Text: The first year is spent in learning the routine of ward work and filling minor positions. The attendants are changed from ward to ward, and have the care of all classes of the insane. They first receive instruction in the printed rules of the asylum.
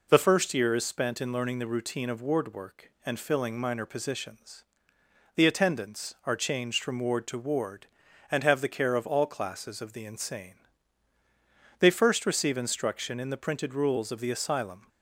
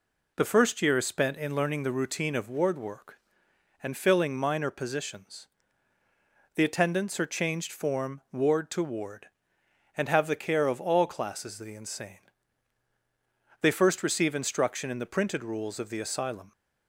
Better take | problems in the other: first | says "form" for "from"; at 7.7 s

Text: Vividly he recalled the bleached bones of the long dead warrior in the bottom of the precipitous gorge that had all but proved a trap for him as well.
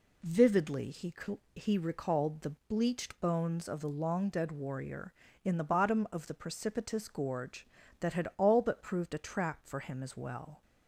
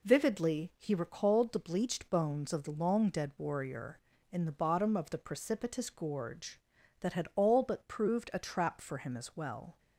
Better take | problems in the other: second | says "he" twice; at 1.5 s

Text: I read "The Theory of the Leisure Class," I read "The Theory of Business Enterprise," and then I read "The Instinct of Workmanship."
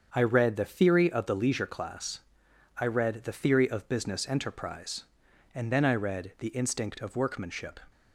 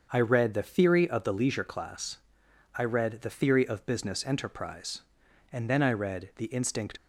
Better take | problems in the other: first | starts louder than the rest; until 1.1 s; 6.5 dB; also in the first // stops before "of Workmanship"; at 6.9 s

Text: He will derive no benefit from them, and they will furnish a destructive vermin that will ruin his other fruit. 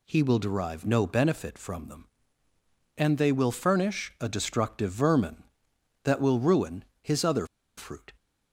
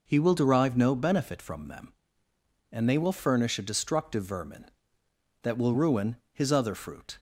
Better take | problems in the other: second | pauses between "ruin" and "his"; slight; at 6.8 s; 0.18 s long; slight in the second // pauses between "other" and "fruit"; slight; at 7.4 s; 0.30 s long

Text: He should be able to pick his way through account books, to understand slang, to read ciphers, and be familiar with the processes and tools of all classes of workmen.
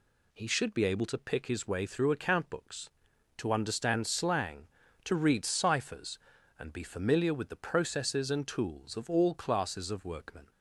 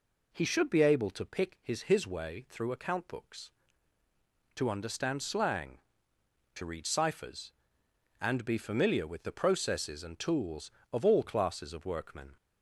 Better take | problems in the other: first | says "his" twice; at 1.8 s

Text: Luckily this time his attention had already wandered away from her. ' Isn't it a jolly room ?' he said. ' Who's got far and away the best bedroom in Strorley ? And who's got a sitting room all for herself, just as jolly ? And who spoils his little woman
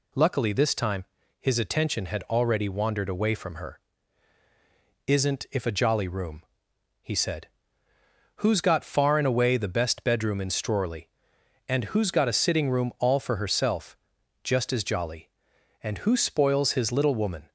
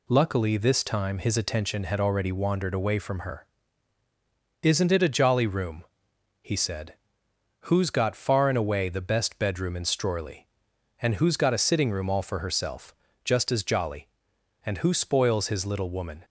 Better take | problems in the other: second | pauses between "time" and "his"; slight; at 1.0 s; 0.34 s long // says "if" for "it"; at 5.5 s

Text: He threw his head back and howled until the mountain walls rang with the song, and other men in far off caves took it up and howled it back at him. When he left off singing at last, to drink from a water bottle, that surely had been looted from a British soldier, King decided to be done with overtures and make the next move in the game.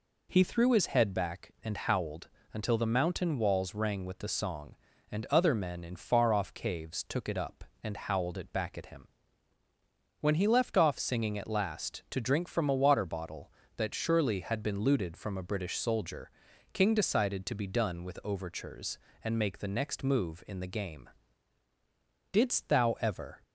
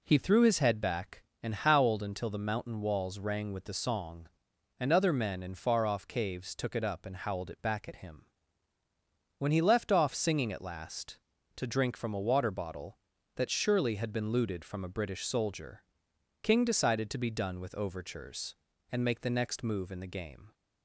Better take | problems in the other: second | pauses between "howled" and "until"; slight; at 2.2 s; 0.26 s long // goes on to say "Didst thou ever"; noticeable; from 22.3 s on; 1.1 s long

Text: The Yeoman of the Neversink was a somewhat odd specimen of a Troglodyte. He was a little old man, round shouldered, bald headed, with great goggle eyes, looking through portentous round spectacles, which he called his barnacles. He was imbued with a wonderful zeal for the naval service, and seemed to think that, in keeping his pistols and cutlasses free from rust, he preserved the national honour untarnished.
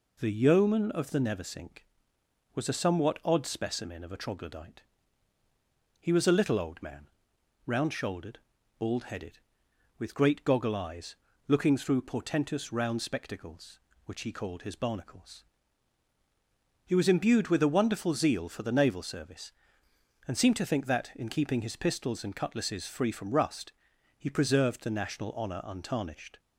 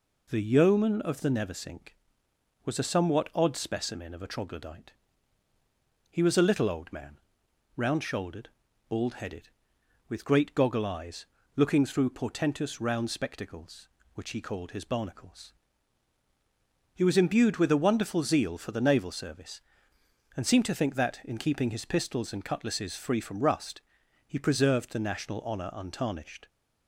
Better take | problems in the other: neither | none

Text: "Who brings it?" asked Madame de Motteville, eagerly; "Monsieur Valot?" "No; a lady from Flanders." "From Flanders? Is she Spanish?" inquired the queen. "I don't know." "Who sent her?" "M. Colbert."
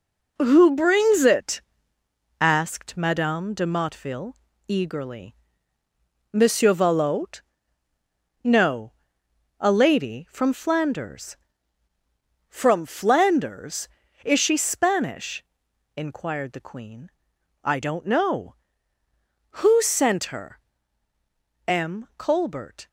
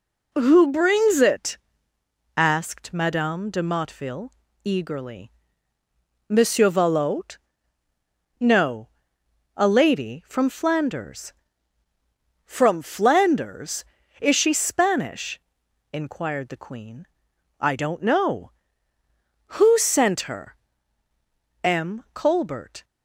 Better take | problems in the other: second | gets quieter; strong; throughout; 7 dB

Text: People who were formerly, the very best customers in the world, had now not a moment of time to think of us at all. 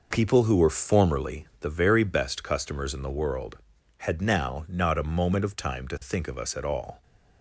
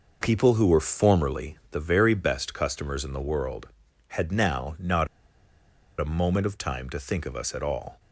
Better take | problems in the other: first | pauses between "not" and "a"; noticeable; at 5.0 s; 0.92 s long

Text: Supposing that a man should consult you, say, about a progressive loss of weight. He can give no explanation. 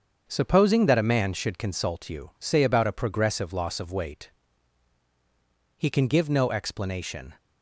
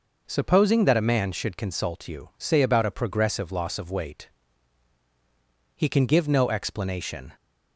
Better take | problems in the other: second | gets quieter; throughout; 7 dB

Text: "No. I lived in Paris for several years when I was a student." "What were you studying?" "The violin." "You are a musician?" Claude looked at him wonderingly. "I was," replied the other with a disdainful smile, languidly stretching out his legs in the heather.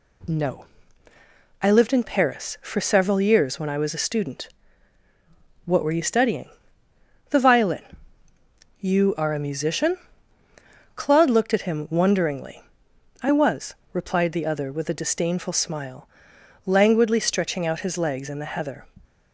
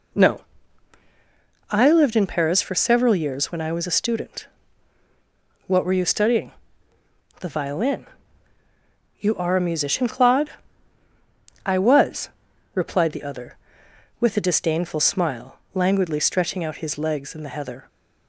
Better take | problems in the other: first | skips "looked at him wonderingly"; at 11.0 s

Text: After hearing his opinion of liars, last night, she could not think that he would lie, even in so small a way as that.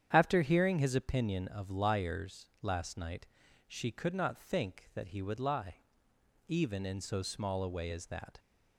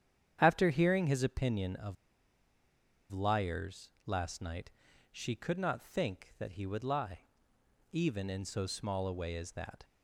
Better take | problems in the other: first | starts louder than the rest; strong; until 1.4 s; 9 dB; strong in the first // pauses between "of" and "liars"; at 1.9 s; 1.1 s long

